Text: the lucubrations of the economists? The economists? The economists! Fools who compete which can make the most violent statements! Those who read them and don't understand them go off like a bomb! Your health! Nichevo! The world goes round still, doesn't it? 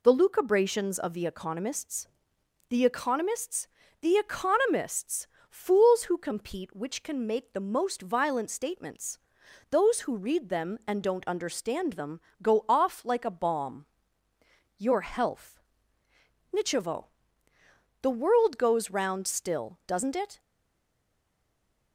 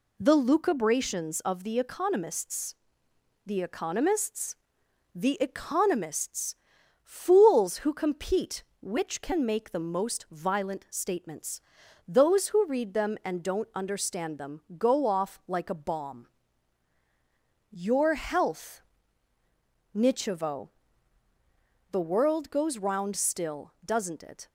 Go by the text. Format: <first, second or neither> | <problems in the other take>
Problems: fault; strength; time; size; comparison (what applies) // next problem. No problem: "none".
second | pauses between "them" and "go"; slight; at 12.1 s; 0.22 s long; slight in the second // stays silent after the last word; noticeable; from 20.3 s on; 1.6 s long